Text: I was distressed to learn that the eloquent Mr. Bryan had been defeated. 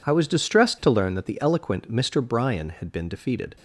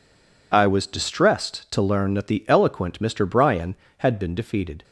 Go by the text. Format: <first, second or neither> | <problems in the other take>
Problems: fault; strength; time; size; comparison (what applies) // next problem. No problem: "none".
first | stays silent before the first word; slight; until 0.5 s; 0.5 s long